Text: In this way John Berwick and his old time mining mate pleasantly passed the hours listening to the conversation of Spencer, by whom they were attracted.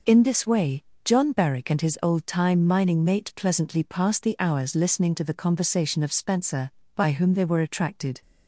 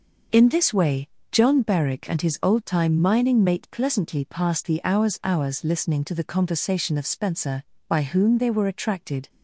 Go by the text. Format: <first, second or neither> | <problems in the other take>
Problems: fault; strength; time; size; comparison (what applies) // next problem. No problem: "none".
first | pauses between "way" and "John"; slight; at 1.0 s; 0.24 s long; slight in the first // says "hours" twice; at 5.2 s